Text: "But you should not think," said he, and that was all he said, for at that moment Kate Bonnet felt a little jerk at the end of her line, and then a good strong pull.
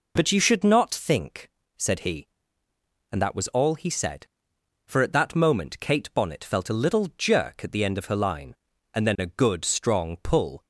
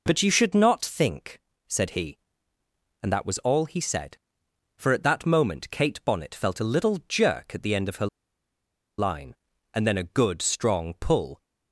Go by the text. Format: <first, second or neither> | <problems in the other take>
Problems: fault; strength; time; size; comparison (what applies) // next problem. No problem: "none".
first | pauses between "her" and "line"; noticeable; at 8.0 s; 0.91 s long